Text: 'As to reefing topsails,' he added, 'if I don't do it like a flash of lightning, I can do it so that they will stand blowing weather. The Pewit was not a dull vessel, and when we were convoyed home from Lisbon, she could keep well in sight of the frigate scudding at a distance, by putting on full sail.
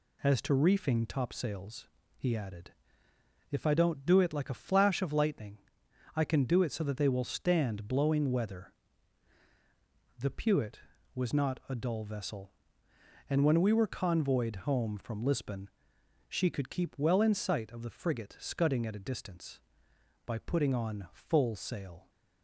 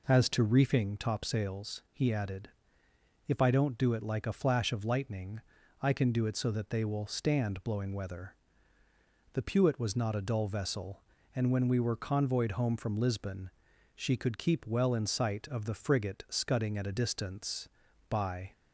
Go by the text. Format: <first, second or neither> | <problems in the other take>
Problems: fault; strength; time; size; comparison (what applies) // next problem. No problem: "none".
first | stops before "putting on full sail"; at 18.5 s